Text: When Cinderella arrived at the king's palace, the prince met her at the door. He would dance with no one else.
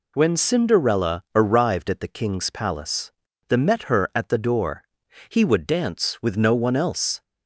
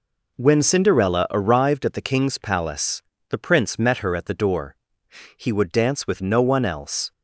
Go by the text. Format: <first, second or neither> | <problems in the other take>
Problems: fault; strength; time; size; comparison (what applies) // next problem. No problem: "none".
second | skips "prince"; at 3.5 s